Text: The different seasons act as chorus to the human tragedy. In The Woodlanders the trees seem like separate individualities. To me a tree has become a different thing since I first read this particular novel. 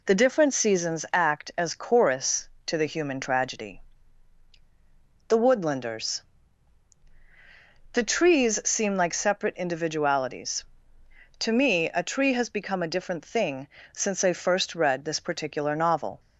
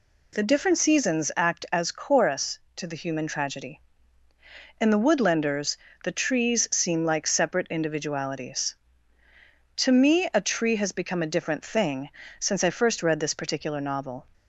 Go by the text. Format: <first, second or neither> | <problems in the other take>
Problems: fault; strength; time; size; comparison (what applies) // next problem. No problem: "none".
second | skips "In"; at 4.5 s // pauses between "Woodlanders" and "the"; strong; at 6.2 s; 1.7 s long; slight in the second // pauses between "thing" and "since"; slight; at 13.6 s; 0.24 s long; slight in the second